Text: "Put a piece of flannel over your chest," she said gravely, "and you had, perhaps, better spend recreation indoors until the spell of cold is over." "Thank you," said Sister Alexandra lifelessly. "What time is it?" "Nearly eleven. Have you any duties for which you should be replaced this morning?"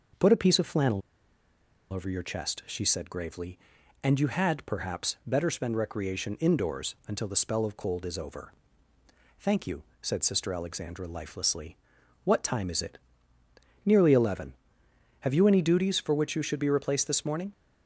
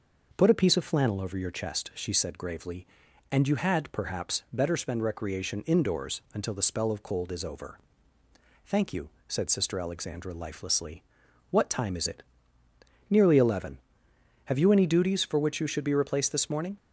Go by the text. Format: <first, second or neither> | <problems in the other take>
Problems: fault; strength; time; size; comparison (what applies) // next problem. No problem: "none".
second | pauses between "flannel" and "over"; noticeable; at 1.0 s; 0.90 s long